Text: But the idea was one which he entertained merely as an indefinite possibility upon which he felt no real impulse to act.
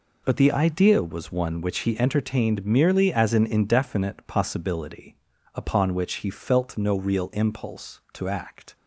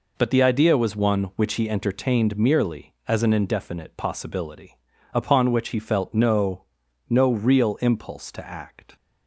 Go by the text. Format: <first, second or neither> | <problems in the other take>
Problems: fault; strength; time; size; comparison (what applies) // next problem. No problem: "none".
first | pauses between "possibility" and "upon"; slight; at 4.7 s; 0.36 s long; also in the first // says "no" twice; at 7.0 s